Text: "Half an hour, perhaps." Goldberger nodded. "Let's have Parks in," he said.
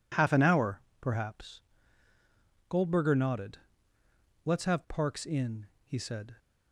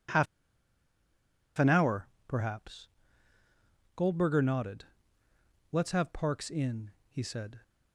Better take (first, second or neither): first